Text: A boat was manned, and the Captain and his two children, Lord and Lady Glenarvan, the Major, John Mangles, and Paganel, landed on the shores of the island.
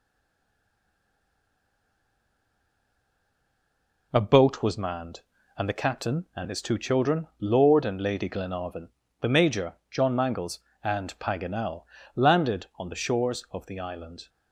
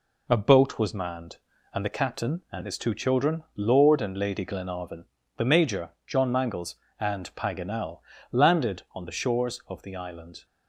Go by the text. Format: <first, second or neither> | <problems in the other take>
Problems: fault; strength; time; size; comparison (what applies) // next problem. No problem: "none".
second | stays silent before the first word; strong; until 4.1 s; 4.1 s long